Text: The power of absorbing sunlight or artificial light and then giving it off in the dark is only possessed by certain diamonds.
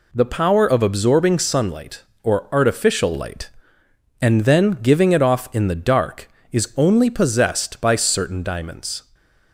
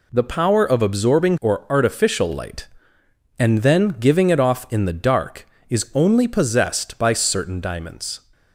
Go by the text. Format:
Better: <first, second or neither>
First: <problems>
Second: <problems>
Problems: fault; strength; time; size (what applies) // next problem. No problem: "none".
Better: first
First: none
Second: skips "sunlight"; at 1.3 s